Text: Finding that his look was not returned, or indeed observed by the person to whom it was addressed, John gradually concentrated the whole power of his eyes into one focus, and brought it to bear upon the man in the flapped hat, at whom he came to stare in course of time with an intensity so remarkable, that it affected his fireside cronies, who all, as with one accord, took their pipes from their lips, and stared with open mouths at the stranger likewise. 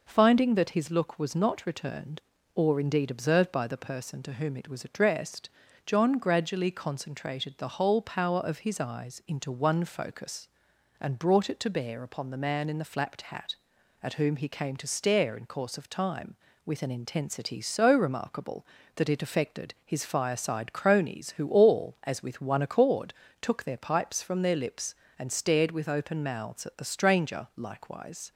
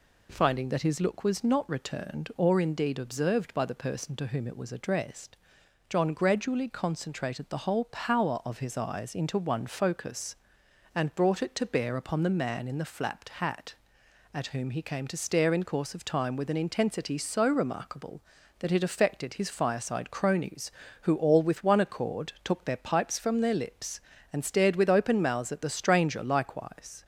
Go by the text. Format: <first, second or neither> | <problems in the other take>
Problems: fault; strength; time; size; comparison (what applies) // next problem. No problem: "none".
first | skips "as"; at 21.4 s